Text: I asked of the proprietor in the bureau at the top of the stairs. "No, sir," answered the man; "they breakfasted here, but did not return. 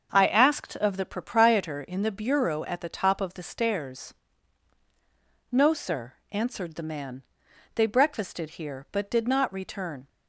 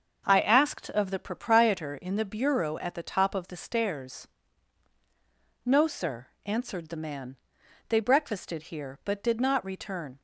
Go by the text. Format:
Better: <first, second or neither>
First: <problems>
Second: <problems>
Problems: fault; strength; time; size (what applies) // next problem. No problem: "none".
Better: neither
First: starts louder than the rest; until 1.1 s; 6.5 dB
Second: starts louder than the rest; until 1.2 s; 6.5 dB